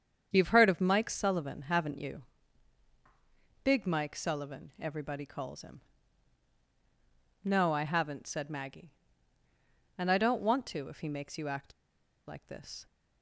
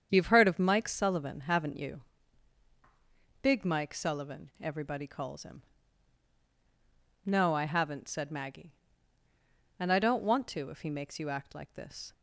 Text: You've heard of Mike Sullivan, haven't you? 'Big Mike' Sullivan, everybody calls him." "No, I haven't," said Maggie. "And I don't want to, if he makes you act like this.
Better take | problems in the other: second | starts louder than the rest; strong; until 1.3 s; 7.5 dB; strong in the second // pauses between "act" and "like"; noticeable; at 11.7 s; 0.54 s long

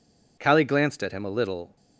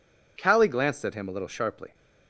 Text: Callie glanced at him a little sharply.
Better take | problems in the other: second | stops before "sharply"; at 1.7 s

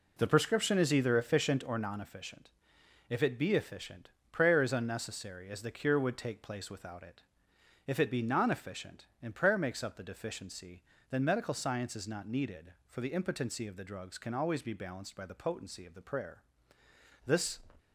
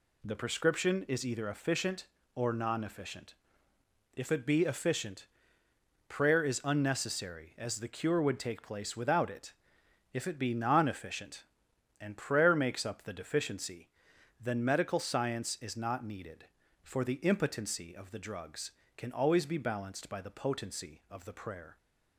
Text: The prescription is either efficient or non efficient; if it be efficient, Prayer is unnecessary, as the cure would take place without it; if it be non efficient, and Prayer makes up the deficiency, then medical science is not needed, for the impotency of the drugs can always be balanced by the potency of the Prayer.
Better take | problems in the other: second | goes on to say "This"; slight; from 17.2 s on; 0.32 s long

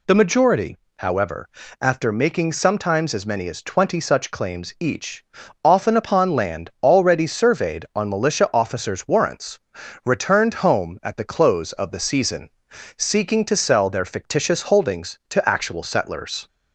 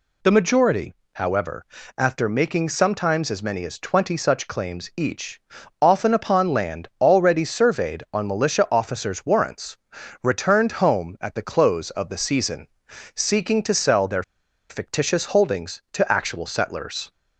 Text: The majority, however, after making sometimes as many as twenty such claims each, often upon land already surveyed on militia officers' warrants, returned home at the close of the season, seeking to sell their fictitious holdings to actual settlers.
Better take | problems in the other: first | pauses between "their" and "fictitious"; noticeable; at 14.2 s; 0.47 s long

